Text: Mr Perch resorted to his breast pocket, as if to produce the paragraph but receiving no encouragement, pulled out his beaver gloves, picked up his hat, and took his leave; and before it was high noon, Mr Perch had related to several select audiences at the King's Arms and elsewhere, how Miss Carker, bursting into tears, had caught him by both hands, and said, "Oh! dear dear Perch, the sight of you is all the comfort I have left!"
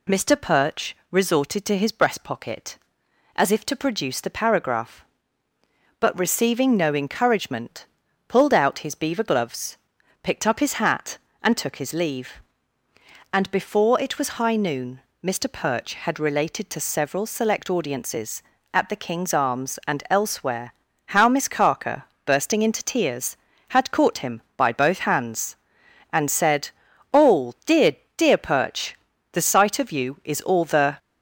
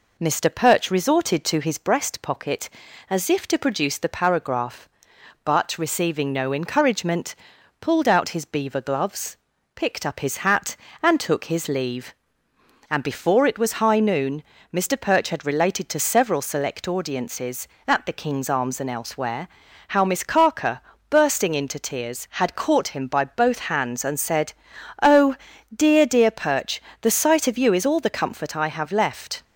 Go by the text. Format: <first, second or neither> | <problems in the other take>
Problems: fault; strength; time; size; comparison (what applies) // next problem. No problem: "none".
second | pauses between "dear" and "dear"; slight; at 27.9 s; 0.20 s long // stops before "comfort I have left"; at 30.9 s